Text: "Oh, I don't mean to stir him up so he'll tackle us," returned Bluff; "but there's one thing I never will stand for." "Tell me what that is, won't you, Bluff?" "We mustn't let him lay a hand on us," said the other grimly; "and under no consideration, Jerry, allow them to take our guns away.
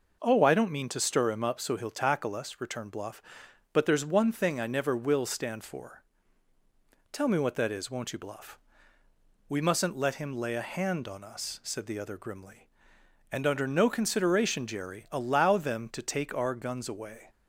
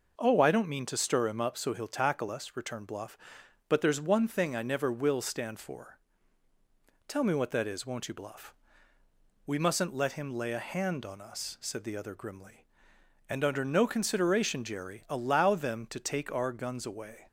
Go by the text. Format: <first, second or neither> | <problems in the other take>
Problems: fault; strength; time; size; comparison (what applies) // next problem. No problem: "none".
neither | none